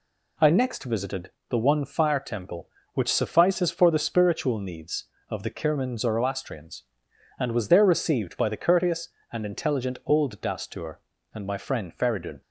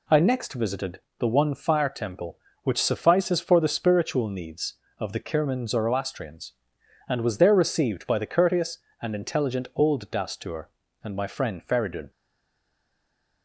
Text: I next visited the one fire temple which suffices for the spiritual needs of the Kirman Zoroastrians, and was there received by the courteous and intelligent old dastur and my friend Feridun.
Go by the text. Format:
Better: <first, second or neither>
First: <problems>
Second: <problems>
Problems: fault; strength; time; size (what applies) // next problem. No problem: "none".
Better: first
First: pauses between "visited" and "the"; slight; at 1.3 s; 0.18 s long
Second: pauses between "visited" and "the"; slight; at 1.0 s; 0.18 s long // stays silent after the last word; noticeable; from 12.1 s on; 1.3 s long